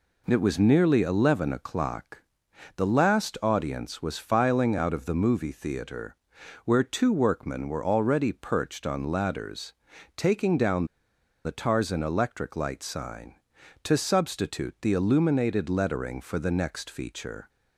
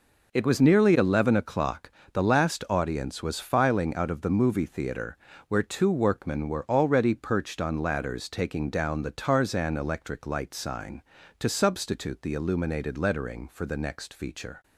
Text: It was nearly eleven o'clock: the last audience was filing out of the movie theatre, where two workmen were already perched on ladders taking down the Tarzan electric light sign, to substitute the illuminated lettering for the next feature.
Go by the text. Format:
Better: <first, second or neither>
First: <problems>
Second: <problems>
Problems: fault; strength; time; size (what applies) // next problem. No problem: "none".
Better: second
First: pauses between "ladders" and "taking"; at 9.7 s; 0.44 s long // pauses between "down" and "the"; noticeable; at 10.8 s; 0.58 s long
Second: none